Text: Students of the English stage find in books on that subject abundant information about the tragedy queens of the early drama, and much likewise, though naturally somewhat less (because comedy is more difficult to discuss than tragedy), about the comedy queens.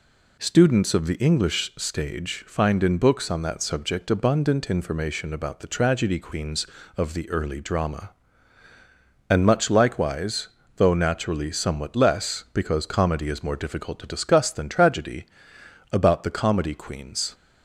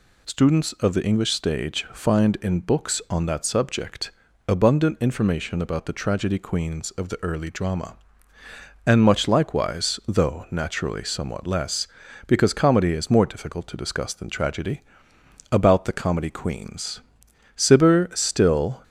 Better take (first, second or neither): first